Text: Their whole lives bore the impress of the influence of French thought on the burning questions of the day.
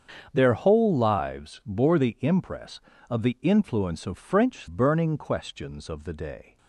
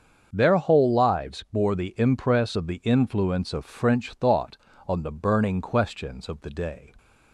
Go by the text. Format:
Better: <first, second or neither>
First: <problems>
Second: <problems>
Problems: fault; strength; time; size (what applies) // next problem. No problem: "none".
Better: second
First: starts louder than the rest; strong; until 1.3 s; 7 dB // skips "thought on the"; at 4.6 s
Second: starts louder than the rest; until 1.3 s; 7 dB